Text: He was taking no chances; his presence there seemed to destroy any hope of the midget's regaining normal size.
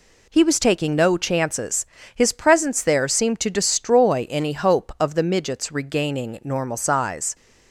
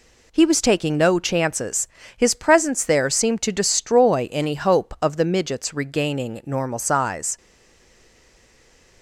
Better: first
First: none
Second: stays silent after the last word; noticeable; from 7.3 s on; 1.7 s long

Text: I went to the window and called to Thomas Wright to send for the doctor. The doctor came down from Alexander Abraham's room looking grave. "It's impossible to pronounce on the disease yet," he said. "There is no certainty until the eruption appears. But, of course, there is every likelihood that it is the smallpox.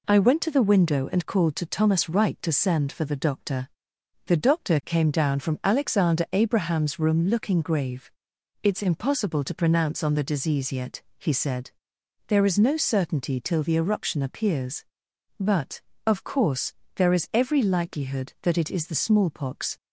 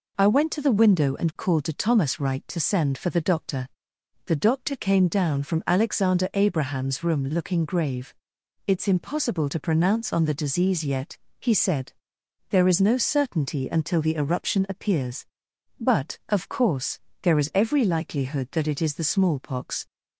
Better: second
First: says "till" for "until"; at 13.4 s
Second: none

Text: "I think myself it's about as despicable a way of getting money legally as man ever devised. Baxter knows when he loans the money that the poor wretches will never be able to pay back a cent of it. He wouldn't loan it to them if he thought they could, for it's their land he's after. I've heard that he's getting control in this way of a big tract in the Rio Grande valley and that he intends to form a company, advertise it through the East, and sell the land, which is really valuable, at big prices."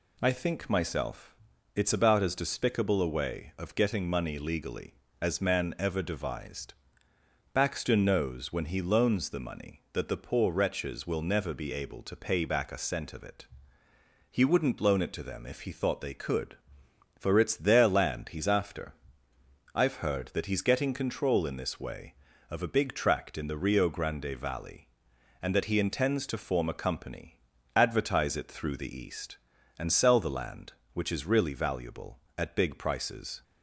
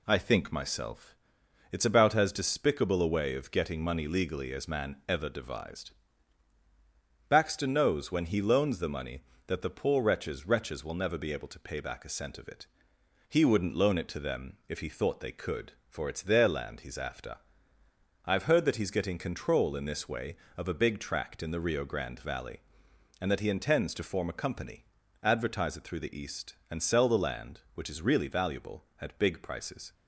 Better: first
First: pauses between "myself" and "it's"; at 1.3 s; 0.40 s long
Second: pauses between "myself" and "it's"; noticeable; at 1.1 s; 0.56 s long // says "wretches" twice; at 10.4 s

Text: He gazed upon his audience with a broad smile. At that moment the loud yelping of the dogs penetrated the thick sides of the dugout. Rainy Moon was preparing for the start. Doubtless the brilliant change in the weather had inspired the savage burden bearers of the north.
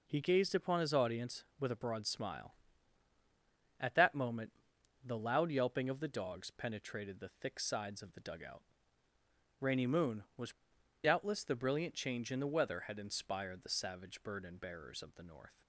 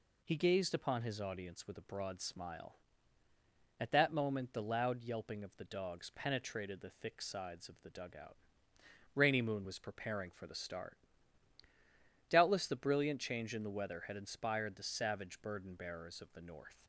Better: second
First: pauses between "moment" and "the"; noticeable; at 4.5 s; 0.52 s long // skips "preparing for the start"; at 10.7 s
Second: none

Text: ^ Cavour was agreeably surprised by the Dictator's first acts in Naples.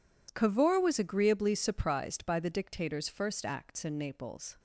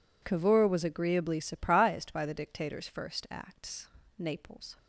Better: first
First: none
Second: skips "in"; at 4.0 s

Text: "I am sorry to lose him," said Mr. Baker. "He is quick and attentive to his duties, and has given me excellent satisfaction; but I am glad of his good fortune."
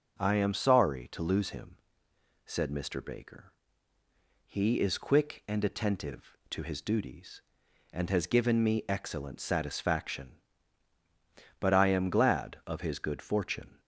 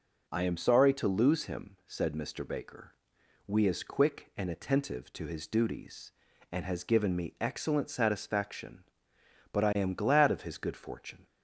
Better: first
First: none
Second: says "We" for "He"; at 3.4 s

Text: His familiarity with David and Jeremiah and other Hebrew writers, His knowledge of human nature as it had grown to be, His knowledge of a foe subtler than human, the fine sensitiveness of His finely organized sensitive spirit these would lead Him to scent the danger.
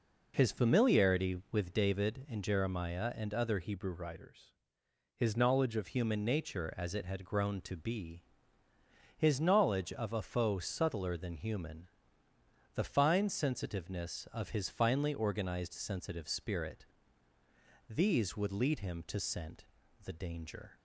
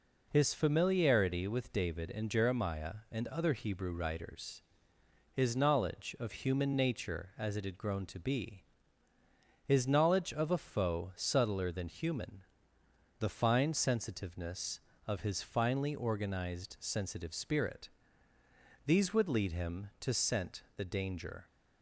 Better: second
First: changes voice from "Hebrew" to "of"; from 3.6 to 5.8 s; 2.2 s long // pauses between "spirit" and "these"; at 16.8 s; 1.0 s long // pauses between "scent" and "the"; at 19.6 s; 0.40 s long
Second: pauses between "spirit" and "these"; noticeable; at 17.8 s; 0.95 s long

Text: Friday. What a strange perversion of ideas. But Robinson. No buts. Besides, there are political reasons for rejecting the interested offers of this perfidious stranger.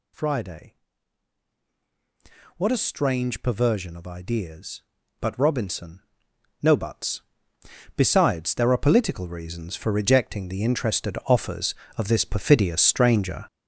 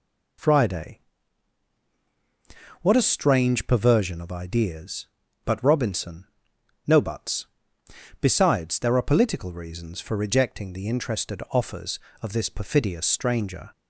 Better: second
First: gets louder; strong; throughout; 9 dB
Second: none

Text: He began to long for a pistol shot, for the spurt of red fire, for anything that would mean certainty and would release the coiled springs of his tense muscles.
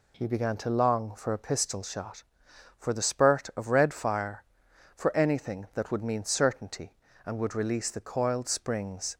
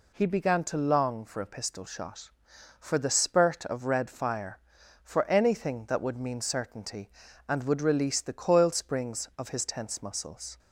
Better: second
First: stops before "of his tense muscles"; at 9.1 s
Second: none

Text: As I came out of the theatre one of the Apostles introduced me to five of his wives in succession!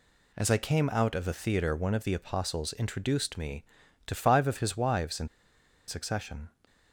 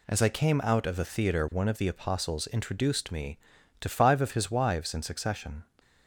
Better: second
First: pauses between "in" and "succession"; noticeable; at 5.2 s; 0.60 s long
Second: none

